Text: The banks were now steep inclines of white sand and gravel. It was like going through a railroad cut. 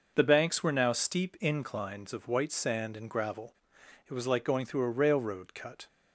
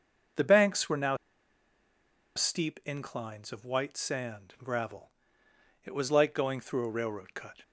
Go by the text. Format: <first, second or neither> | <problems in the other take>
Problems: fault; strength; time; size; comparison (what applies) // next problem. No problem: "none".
first | starts louder than the rest; until 2.6 s; 6 dB // pauses between "now" and "steep"; at 1.1 s; 1.1 s long